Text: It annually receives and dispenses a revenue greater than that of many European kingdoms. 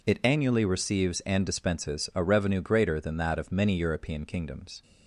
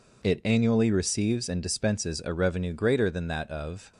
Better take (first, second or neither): first